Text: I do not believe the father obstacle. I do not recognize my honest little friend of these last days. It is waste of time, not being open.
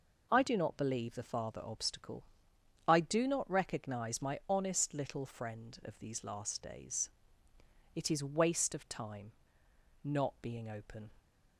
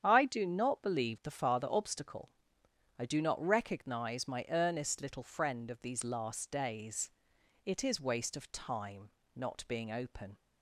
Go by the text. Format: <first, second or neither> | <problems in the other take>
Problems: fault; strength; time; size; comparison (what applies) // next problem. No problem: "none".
first | starts louder than the rest; strong; until 1.0 s; 8.5 dB // says "earnest" for "honest"; at 4.4 s